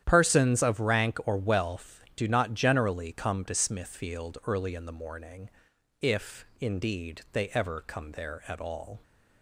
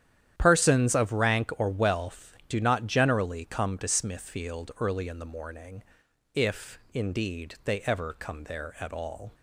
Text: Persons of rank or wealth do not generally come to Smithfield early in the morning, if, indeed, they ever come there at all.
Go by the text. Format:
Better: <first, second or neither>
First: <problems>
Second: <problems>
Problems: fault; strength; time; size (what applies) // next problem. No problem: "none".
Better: neither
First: starts louder than the rest; strong; until 1.0 s; 10.5 dB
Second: starts louder than the rest; strong; until 1.3 s; 10 dB